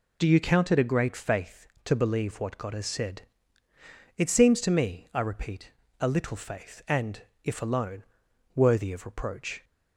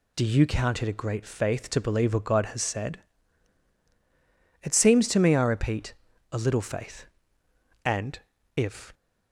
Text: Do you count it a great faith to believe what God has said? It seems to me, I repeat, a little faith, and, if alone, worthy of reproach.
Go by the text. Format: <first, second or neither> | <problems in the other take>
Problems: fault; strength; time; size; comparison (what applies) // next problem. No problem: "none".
first | stops before "alone worthy of reproach"; at 8.9 s